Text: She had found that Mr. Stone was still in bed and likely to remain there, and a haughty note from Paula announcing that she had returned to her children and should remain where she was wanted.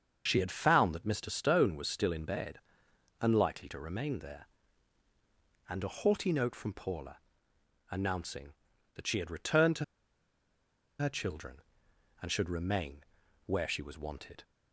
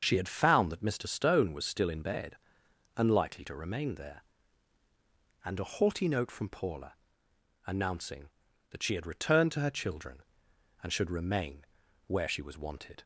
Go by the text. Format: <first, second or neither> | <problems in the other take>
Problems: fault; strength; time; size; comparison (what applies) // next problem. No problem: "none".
second | starts louder than the rest; until 1.2 s; 6.5 dB; also in the second // pauses between "Paula" and "announcing"; noticeable; at 7.1 s; 0.72 s long; noticeable in the second // pauses between "to" and "her"; at 9.8 s; 1.1 s long // pauses between "remain" and "where"; at 13.0 s; 0.44 s long; also in the second